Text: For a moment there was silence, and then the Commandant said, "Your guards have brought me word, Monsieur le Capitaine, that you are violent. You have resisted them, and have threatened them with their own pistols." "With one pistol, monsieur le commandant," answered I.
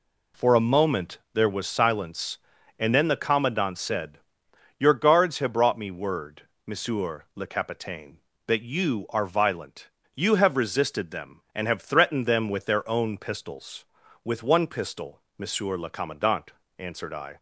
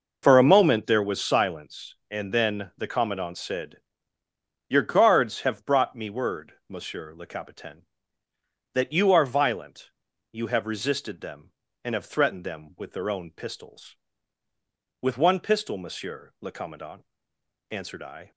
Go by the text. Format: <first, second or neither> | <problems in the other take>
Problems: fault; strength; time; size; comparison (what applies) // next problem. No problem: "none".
neither | none